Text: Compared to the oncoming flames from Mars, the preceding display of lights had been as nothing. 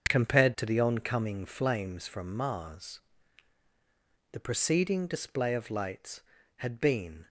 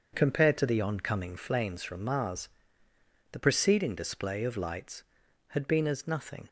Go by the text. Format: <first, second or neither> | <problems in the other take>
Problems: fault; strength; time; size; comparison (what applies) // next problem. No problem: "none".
second | starts louder than the rest; until 1.1 s; 6.5 dB; also in the second // stops before "as nothing"; at 7.2 s